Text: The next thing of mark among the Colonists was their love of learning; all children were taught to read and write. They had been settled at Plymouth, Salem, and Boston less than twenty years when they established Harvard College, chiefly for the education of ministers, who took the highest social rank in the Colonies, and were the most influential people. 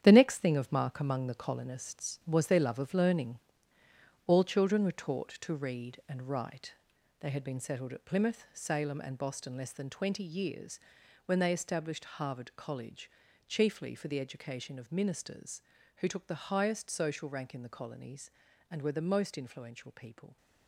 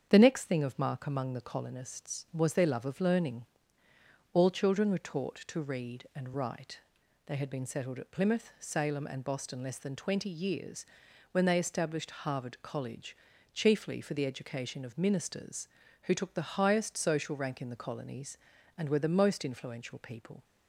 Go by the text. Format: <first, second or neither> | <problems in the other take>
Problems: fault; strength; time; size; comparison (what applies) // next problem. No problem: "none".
second | gets quieter; strong; throughout; 9 dB // starts louder than the rest; strong; until 1.0 s; 9.5 dB; strong in the second // pauses between "years" and "when"; noticeable; at 10.7 s; 0.48 s long; noticeable in the second